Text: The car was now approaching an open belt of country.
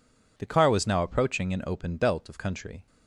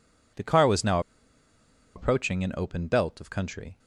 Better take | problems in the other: first | pauses between "now" and "approaching"; noticeable; at 0.9 s; 0.96 s long

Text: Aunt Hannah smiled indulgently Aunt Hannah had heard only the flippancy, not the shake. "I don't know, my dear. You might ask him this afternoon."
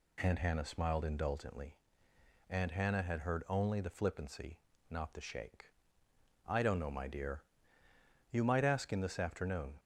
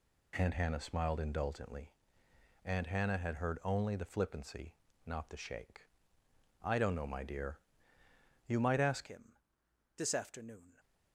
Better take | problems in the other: first | pauses between "indulgently" and "Aunt"; noticeable; at 1.9 s; 0.74 s long; noticeable in the first // changes voice at "him"; from 9.0 s on; 1.7 s long // pauses between "him" and "this"; noticeable; at 9.3 s; 0.60 s long

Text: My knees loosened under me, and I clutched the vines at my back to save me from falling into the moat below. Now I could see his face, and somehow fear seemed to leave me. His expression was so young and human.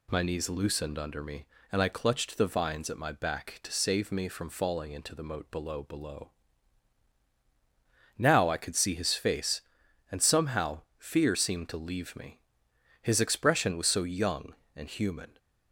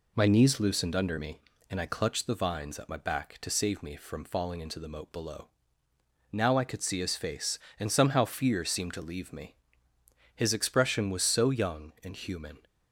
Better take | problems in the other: second | says "below" twice; at 5.8 s // pauses between "somehow" and "fear"; slight; at 10.8 s; 0.16 s long

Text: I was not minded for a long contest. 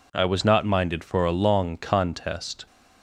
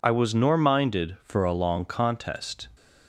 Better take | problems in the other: first | says "nor" for "not"; at 0.3 s

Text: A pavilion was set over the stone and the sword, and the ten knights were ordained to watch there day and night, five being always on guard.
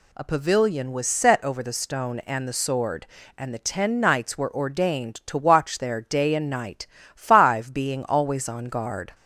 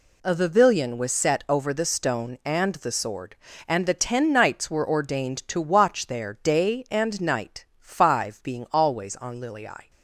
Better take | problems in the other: first | says "lilii" for "guard"; at 9.3 s

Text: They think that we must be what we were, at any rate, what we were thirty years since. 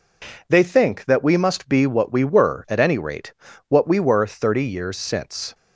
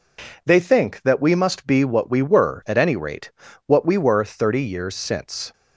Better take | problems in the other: neither | none

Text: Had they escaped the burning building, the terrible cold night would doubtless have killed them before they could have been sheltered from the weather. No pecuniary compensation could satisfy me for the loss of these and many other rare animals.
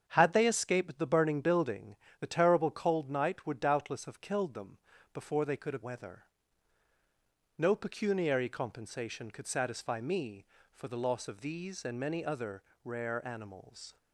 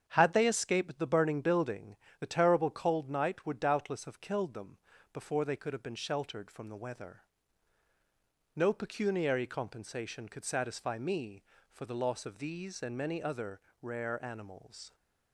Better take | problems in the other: second | starts louder than the rest; strong; until 1.0 s; 7.5 dB; strong in the second // pauses between "them" and "before"; slight; at 4.7 s; 0.36 s long; slight in the second // skips "been sheltered from the"; at 5.8 s // pauses between "other" and "rare"; slight; at 12.6 s; 0.22 s long; slight in the second

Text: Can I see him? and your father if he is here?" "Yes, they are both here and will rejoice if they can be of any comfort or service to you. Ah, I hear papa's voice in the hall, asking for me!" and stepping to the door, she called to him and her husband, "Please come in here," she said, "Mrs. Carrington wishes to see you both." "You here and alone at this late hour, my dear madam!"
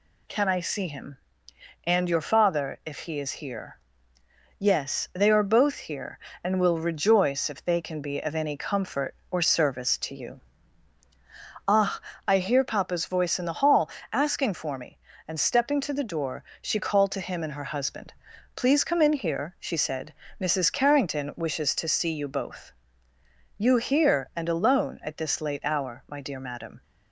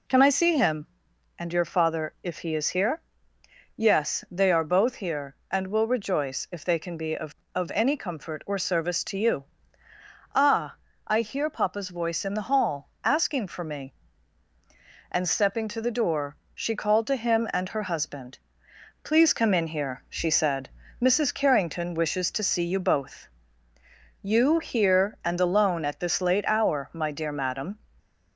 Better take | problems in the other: first | says "of" twice; at 7.5 s

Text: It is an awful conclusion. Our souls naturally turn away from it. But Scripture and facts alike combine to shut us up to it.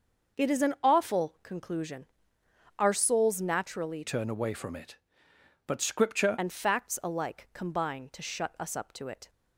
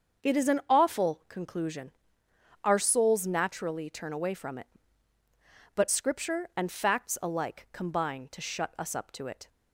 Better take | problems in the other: second | starts louder than the rest; noticeable; until 1.4 s; 6 dB; also in the second // changes voice from "turn" to "Scripture"; from 4.0 to 6.3 s; 2.3 s long

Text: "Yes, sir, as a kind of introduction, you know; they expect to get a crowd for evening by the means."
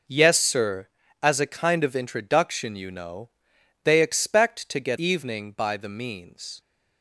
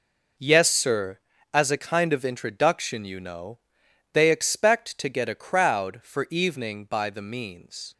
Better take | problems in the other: second | skips "a crowd for"; at 4.9 s

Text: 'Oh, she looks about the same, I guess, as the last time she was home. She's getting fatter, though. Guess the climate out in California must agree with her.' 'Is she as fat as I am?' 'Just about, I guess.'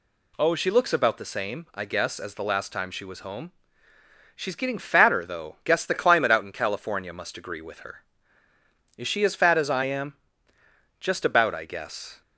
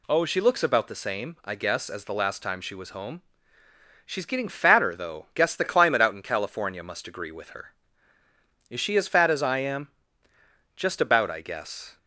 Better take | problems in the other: neither | none

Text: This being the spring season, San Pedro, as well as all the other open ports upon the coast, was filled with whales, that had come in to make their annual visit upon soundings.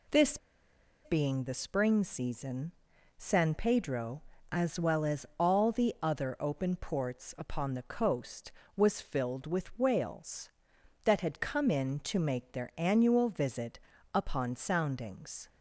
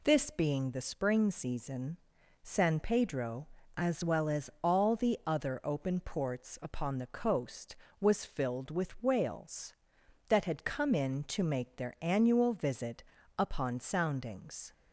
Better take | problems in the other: second | pauses between "This" and "being"; noticeable; at 0.3 s; 0.68 s long // pauses between "visit" and "upon"; slight; at 13.7 s; 0.36 s long; slight in the second

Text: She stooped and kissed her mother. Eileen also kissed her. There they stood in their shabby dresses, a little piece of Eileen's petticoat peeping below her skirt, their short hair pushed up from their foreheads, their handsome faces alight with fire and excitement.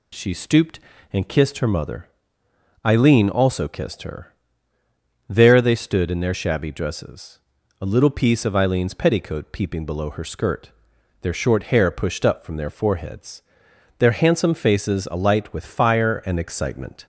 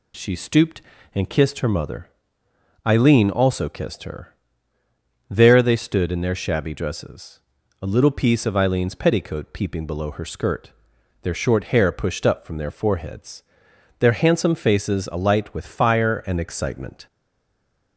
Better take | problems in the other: first | stays silent after the last word; slight; from 17.0 s on; 0.9 s long

